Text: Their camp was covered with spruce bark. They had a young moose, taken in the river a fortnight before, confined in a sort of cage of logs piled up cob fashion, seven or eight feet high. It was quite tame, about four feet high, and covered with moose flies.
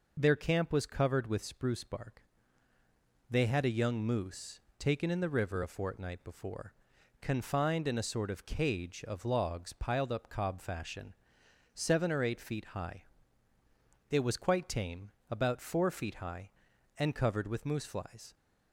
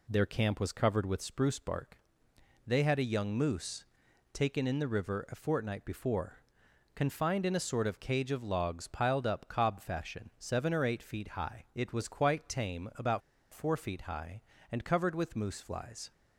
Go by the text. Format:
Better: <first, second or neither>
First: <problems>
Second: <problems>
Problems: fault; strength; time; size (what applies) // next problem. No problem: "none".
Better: first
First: none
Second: pauses between "about" and "four"; slight; at 13.2 s; 0.32 s long